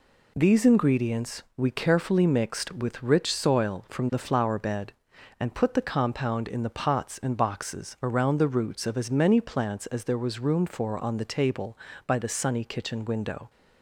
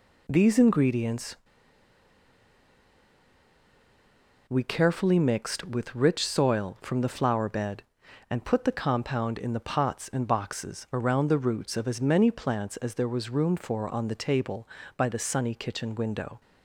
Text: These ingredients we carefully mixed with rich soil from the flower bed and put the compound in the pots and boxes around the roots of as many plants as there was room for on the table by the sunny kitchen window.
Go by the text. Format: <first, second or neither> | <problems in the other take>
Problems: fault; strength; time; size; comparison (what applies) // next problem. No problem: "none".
first | pauses between "ingredients" and "we"; strong; at 1.3 s; 3.1 s long